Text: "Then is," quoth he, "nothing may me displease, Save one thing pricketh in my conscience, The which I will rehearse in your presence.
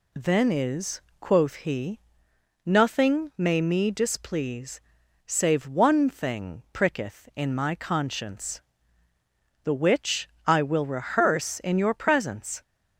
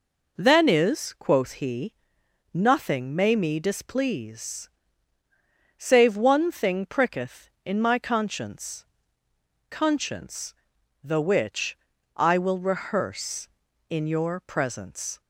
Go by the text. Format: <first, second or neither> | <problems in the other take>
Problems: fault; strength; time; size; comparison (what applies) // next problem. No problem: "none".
first | says "conscience" twice; at 9.7 s // pauses between "which" and "I"; slight; at 11.7 s; 0.36 s long; slight in the first